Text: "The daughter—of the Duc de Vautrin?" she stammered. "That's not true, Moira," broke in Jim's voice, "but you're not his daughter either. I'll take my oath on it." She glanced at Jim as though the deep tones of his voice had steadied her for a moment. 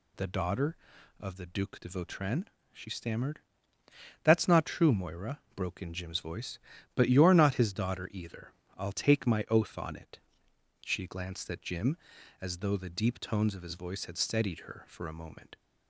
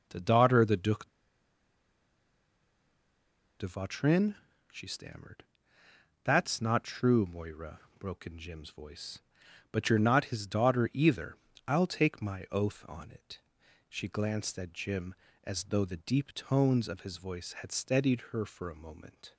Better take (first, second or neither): first